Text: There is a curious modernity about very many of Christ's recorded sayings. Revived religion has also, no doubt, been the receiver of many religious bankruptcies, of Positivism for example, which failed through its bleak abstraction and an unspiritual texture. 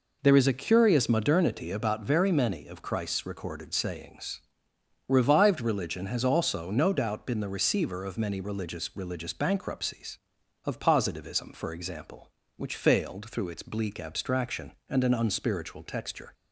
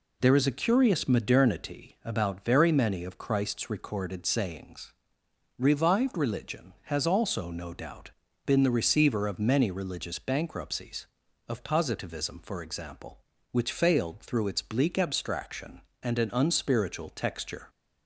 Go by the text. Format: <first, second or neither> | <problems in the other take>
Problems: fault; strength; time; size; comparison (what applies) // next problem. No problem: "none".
second | says "religious" twice; at 8.9 s